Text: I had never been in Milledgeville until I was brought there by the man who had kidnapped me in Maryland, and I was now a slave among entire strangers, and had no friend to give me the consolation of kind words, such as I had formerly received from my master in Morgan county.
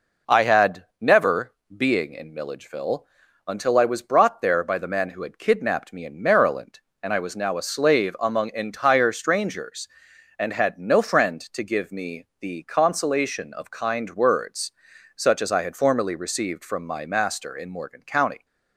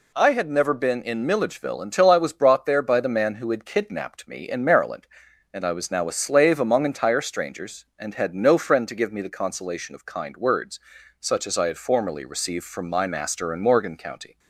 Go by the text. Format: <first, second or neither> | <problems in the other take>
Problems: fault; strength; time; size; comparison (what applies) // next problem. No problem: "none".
second | pauses between "had" and "never"; slight; at 0.8 s; 0.16 s long // says "being" for "been"; at 1.7 s // pauses between "Milledgeville" and "until"; at 3.0 s; 0.42 s long // pauses between "me" and "the"; slight; at 12.2 s; 0.16 s long